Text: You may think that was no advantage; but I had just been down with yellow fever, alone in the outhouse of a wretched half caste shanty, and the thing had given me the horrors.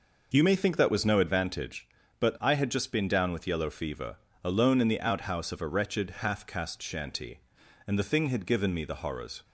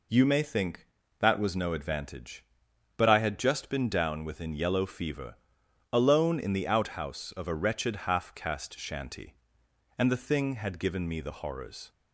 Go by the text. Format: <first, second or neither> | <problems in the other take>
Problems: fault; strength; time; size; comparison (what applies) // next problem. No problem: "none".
first | says "within" for "with"; at 4.2 s